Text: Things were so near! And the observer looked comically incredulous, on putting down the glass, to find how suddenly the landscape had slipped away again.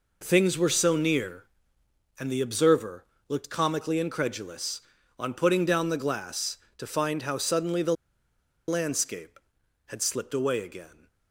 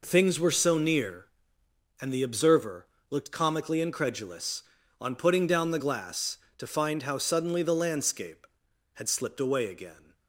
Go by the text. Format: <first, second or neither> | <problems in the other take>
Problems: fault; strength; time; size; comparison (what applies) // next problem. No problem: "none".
second | pauses between "observer" and "looked"; slight; at 3.0 s; 0.24 s long; slight in the second // pauses between "the" and "landscape"; noticeable; at 7.9 s; 0.73 s long